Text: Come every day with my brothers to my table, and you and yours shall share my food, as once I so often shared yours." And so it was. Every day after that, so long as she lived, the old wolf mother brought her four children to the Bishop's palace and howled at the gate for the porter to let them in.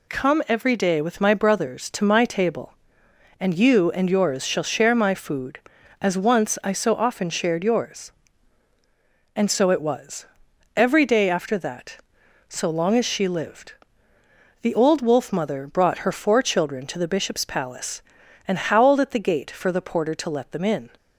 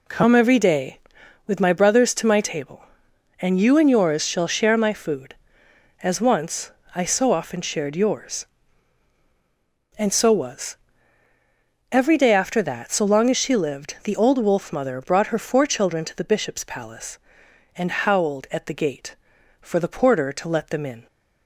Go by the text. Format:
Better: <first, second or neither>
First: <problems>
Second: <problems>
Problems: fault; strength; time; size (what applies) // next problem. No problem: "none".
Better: first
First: none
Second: pauses between "once" and "I"; slight; at 6.7 s; 0.24 s long // skips "it"; at 10.3 s